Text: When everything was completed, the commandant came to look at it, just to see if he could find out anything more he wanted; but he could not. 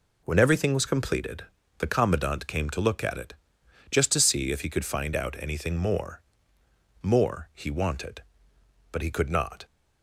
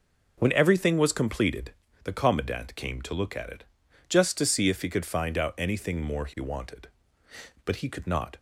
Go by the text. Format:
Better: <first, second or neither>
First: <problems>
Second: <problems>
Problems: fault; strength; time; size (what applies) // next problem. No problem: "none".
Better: second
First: says "more" twice; at 7.0 s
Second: none